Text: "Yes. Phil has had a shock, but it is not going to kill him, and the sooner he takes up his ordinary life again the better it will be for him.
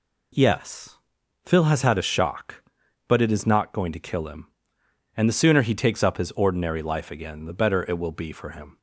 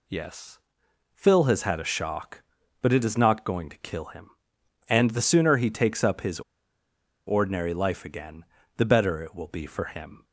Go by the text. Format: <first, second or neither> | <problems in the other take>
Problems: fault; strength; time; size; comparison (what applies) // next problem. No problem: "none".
first | pauses between "his" and "ordinary"; noticeable; at 6.3 s; 0.88 s long // pauses between "again" and "the"; slight; at 8.4 s; 0.32 s long